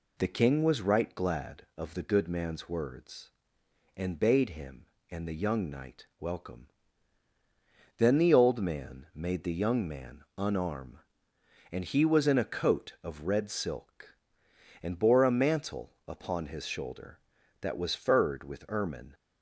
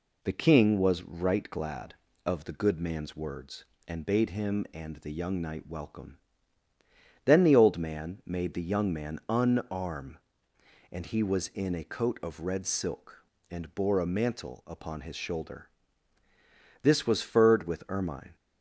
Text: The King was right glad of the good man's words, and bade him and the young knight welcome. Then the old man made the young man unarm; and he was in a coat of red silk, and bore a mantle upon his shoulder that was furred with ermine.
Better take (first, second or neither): first